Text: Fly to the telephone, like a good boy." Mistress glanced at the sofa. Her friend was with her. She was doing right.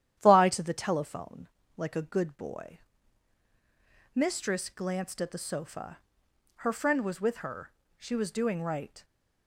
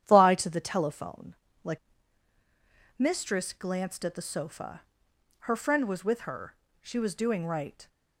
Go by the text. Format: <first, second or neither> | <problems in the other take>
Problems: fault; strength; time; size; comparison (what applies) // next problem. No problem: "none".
first | starts louder than the rest; strong; until 1.0 s; 10 dB; strong in the first // skips "a good boy"; at 2.3 s